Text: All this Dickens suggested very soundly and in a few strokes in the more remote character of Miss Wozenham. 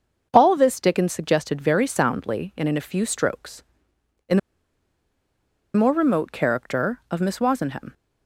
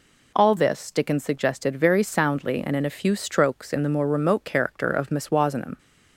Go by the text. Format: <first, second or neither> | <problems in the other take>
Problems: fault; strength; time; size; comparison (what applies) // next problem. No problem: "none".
second | starts louder than the rest; until 1.3 s; 6.5 dB // pauses between "the" and "more"; strong; at 4.3 s; 1.3 s long